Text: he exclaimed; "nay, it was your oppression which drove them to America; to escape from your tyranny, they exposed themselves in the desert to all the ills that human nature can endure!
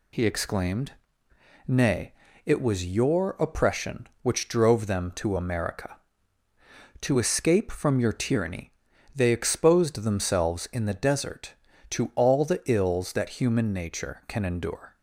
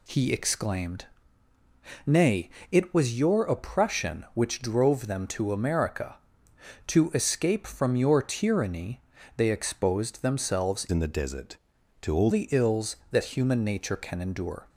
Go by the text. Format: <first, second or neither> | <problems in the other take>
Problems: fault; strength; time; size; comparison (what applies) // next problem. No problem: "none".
first | changes voice from "in" to "all"; from 10.8 to 12.2 s; 1.4 s long